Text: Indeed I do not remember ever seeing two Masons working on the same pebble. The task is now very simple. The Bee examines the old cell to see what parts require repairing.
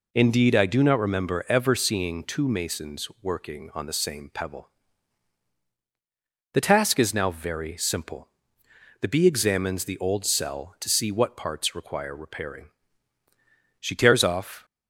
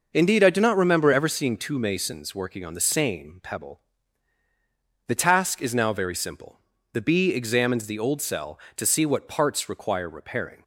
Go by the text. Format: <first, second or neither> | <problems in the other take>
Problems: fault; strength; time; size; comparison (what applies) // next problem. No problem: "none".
second | goes on to say "She tears off"; noticeable; from 13.7 s on; 0.86 s long